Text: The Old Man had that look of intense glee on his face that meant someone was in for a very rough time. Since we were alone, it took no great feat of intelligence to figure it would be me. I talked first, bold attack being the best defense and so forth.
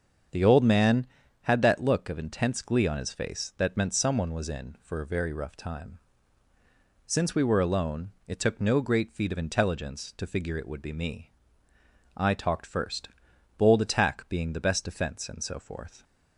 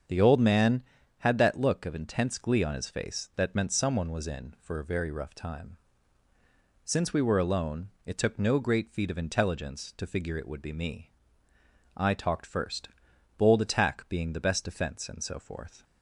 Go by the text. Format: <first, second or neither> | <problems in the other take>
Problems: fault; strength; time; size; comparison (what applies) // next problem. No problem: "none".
neither | starts louder than the rest; the same in both